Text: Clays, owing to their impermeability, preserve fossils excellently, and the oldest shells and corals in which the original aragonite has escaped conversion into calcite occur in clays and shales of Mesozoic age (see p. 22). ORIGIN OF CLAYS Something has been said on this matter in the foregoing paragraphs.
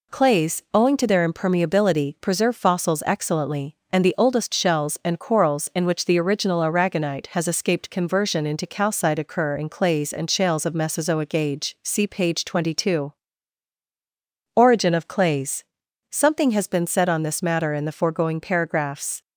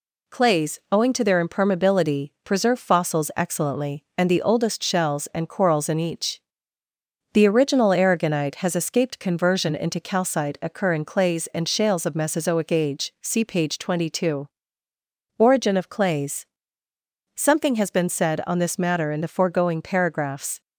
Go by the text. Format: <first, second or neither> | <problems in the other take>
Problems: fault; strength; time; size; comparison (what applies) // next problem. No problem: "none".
first | says "each" for "which"; at 5.9 s // pauses between "CLAYS" and "Something"; noticeable; at 16.4 s; 0.88 s long; noticeable in the first